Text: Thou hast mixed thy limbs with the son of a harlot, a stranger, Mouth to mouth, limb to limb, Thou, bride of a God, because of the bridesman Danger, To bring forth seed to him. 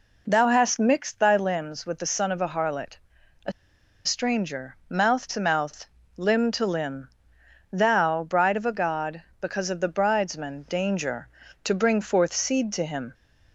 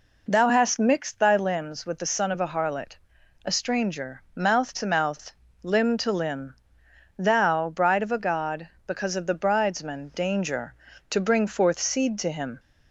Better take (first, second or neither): second